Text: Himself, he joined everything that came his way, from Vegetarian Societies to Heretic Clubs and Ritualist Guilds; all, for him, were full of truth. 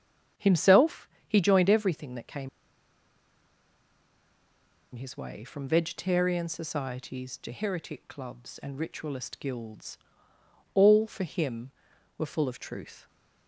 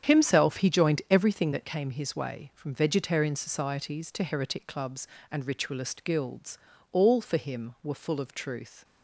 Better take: second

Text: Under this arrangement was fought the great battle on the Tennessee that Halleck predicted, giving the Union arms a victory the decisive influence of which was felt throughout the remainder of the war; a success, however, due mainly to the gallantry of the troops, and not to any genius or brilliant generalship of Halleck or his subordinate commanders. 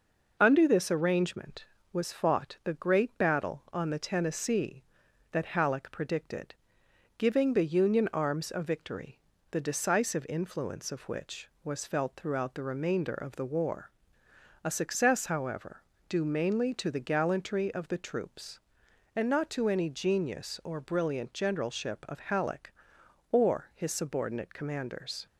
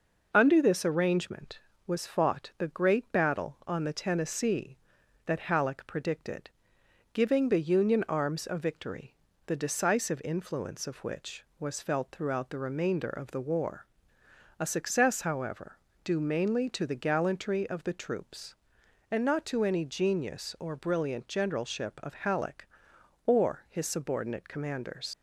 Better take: first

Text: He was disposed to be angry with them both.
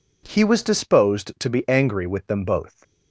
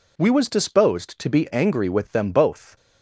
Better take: first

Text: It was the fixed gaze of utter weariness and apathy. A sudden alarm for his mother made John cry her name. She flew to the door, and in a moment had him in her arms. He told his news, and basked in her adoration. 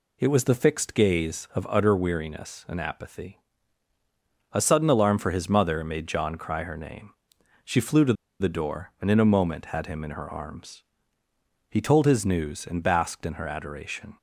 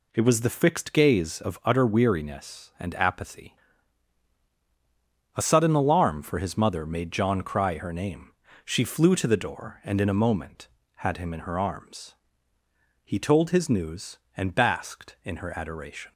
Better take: second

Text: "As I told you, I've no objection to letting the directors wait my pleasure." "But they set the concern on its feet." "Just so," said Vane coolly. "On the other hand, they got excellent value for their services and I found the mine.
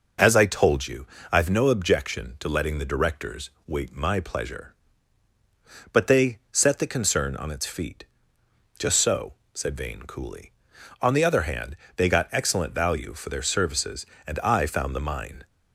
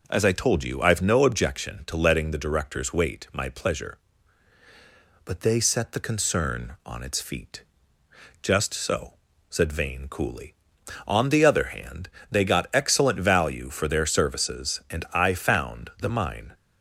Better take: neither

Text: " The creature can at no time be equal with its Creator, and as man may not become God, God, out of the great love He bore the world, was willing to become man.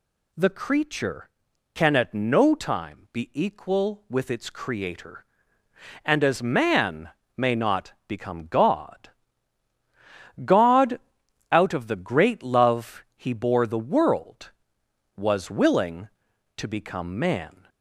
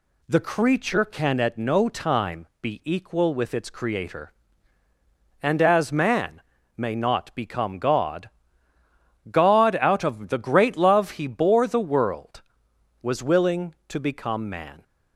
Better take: neither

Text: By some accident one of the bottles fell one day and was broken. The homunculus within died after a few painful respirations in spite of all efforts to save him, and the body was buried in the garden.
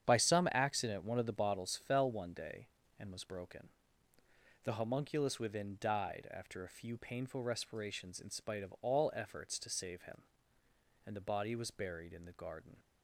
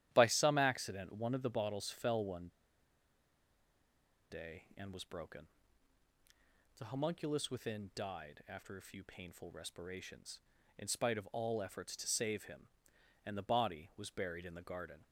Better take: first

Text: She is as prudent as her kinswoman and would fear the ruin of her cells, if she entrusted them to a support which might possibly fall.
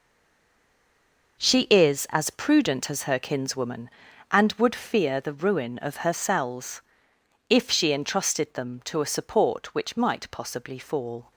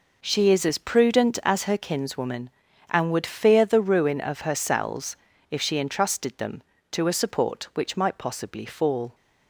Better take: second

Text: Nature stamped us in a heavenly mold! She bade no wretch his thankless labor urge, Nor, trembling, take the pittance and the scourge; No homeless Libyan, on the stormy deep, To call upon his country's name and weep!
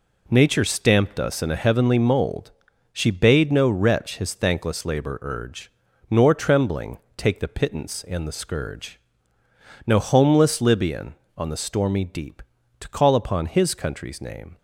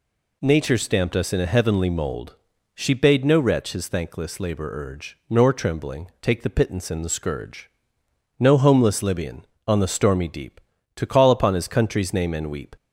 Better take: second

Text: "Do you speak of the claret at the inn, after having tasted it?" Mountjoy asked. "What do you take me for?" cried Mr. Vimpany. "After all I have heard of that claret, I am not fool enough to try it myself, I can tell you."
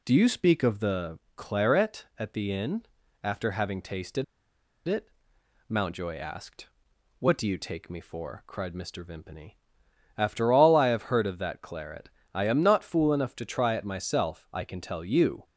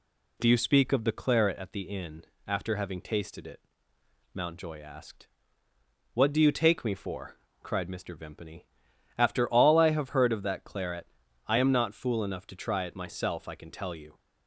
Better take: second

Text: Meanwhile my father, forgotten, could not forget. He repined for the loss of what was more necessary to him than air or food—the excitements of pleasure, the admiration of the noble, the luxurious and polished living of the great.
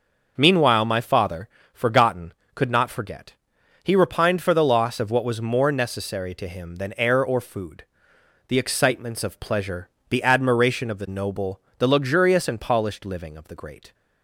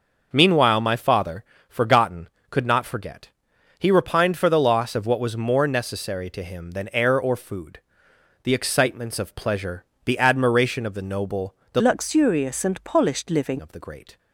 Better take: first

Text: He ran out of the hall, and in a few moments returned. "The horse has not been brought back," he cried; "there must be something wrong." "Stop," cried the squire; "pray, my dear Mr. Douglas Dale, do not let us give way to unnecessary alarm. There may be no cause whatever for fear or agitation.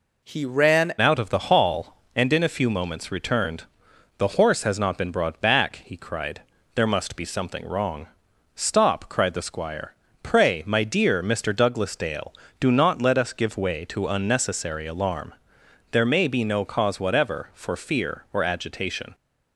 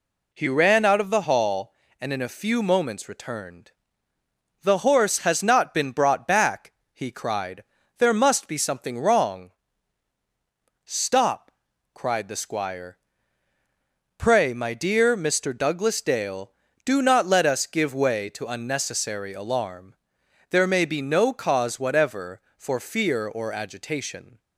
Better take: second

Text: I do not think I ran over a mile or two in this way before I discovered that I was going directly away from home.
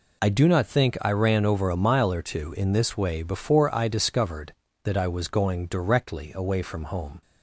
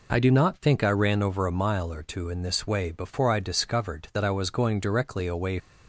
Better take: first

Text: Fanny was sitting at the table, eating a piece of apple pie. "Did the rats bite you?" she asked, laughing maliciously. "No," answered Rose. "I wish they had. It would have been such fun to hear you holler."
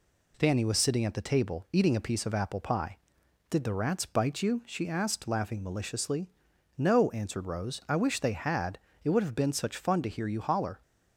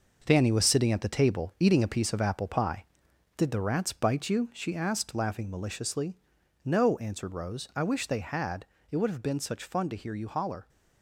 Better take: first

